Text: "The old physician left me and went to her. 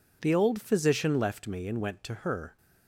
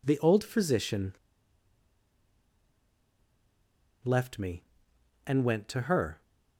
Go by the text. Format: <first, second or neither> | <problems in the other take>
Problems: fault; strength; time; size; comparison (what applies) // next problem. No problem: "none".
first | pauses between "physician" and "left"; strong; at 1.1 s; 2.9 s long